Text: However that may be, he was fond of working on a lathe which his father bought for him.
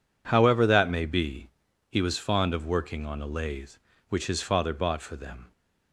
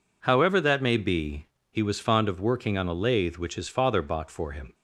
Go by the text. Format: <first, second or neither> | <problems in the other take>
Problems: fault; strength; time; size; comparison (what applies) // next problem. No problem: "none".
second | says "them" for "him"; at 5.1 s